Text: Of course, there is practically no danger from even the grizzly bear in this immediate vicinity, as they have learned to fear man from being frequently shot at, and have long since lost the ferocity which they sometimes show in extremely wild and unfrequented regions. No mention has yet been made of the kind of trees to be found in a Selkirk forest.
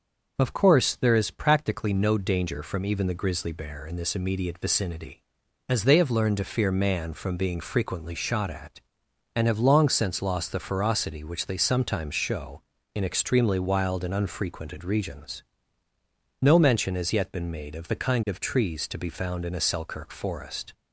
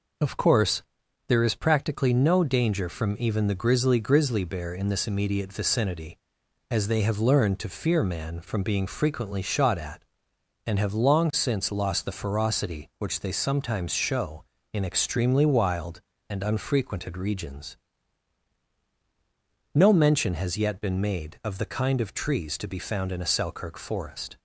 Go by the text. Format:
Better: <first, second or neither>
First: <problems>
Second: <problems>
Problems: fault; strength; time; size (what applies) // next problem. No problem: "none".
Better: first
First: none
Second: says "grizzly" twice; at 3.9 s